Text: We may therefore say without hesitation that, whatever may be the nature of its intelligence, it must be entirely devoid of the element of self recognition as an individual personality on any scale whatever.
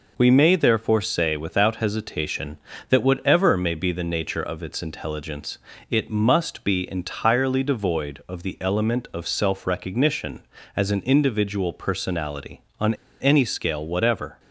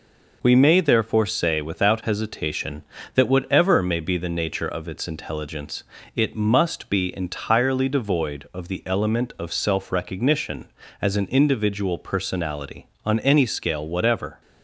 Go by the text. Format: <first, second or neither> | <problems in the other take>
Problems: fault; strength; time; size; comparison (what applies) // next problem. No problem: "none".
second | pauses between "on" and "any"; slight; at 12.9 s; 0.25 s long